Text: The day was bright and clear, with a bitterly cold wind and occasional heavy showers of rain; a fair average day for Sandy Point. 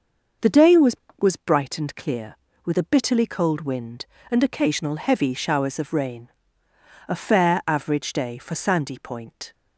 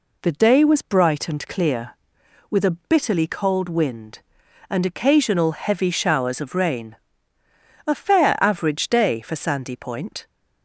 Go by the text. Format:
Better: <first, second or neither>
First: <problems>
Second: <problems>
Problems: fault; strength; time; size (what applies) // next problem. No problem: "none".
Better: second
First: says "was" twice; at 1.1 s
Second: none